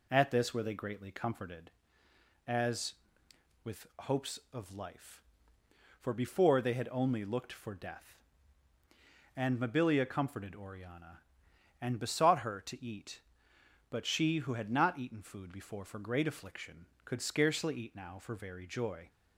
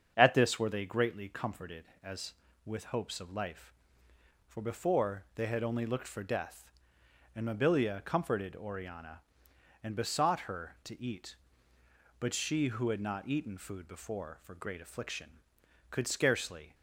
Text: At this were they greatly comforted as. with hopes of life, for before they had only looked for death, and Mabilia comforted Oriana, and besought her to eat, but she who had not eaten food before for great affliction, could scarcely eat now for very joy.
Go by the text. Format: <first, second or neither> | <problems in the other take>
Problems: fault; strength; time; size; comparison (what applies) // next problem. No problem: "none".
first | starts louder than the rest; strong; until 1.1 s; 7.5 dB // stops before "eat now for very joy"; at 16.7 s